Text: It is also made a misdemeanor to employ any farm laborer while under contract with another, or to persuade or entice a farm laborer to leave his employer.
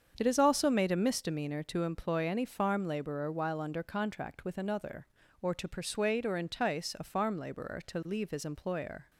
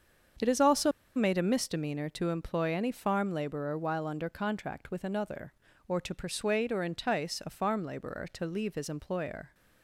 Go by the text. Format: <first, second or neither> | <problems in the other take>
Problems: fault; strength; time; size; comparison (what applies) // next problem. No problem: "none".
first | starts louder than the rest; strong; until 1.6 s; 7.5 dB; strong in the first // pauses between "also" and "made"; slight; at 0.9 s; 0.24 s long